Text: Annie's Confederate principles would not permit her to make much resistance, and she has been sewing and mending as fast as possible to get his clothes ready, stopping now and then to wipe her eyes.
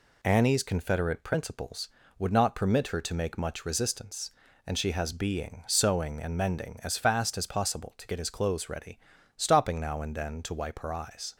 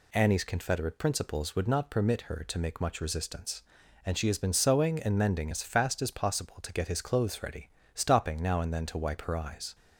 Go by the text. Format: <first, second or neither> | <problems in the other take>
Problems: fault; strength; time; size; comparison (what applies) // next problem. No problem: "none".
second | says "being" for "been"; at 5.1 s